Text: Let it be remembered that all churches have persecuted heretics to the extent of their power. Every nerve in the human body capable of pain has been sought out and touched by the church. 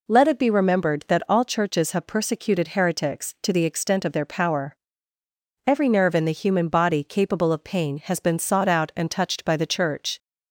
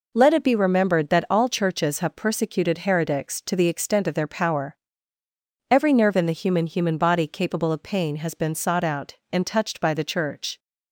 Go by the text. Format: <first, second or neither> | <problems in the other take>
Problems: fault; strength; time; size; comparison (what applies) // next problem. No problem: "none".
first | says "human" twice; at 6.6 s